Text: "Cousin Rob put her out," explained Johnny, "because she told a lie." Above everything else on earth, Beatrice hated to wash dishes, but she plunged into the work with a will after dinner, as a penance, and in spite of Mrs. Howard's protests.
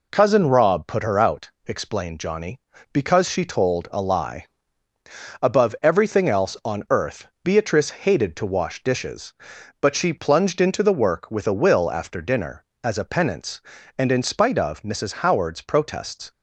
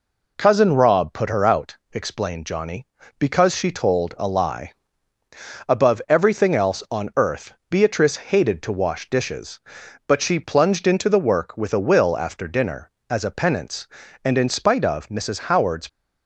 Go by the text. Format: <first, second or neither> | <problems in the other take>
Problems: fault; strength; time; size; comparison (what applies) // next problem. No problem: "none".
first | stops before "protests"; at 15.8 s